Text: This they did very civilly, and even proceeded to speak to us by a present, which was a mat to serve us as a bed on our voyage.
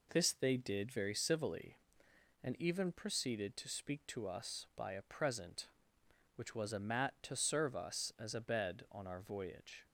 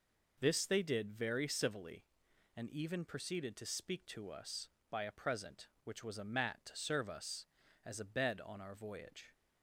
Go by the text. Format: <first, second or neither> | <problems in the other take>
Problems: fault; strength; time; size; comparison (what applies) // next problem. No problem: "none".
neither | none